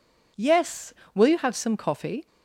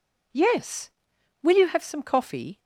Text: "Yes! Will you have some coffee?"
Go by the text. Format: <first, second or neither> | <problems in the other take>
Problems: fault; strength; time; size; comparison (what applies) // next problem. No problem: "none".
neither | none